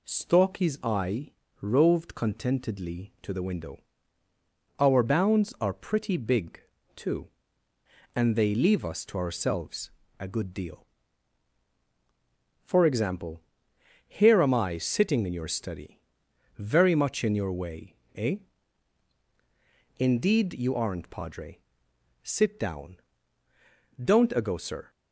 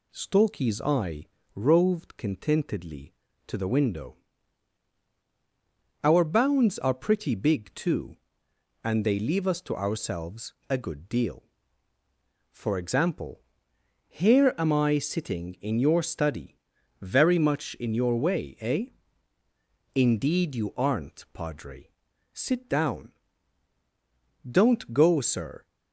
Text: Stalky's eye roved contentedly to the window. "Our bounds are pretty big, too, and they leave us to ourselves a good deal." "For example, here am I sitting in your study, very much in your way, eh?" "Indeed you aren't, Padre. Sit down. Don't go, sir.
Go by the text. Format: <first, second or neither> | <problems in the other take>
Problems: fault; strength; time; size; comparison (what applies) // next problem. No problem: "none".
second | pauses between "eye" and "roved"; slight; at 1.2 s; 0.32 s long; slight in the second // pauses between "ourselves" and "a"; slight; at 9.8 s; 0.30 s long; slight in the second // says "ago" for "go"; at 24.3 s